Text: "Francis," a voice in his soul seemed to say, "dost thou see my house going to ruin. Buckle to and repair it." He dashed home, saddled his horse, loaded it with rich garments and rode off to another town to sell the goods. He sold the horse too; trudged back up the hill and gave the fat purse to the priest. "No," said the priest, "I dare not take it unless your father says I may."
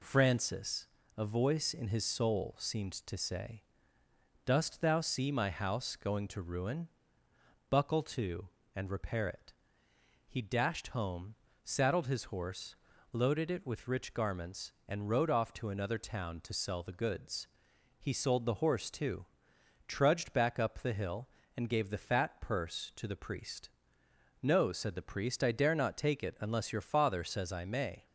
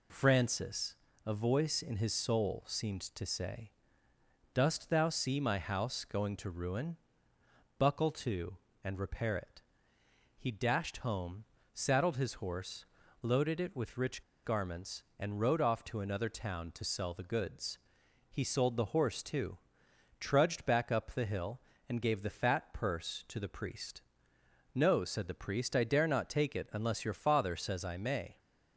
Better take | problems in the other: first | pauses between "rich" and "garments"; slight; at 14.2 s; 0.23 s long

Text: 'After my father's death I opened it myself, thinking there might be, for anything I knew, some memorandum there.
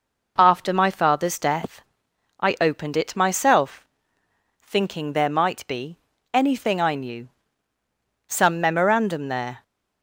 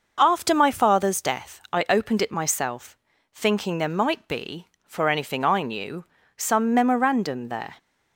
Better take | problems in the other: second | pauses between "death" and "I"; noticeable; at 1.8 s; 0.58 s long // skips "for"; at 6.1 s

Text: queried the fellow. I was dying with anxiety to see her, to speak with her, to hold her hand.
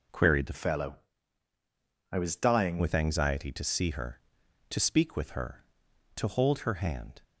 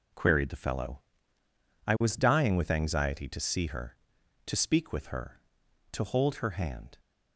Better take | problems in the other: second | changes voice from "fellow" to "dying"; from 0.5 to 2.7 s; 2.2 s long

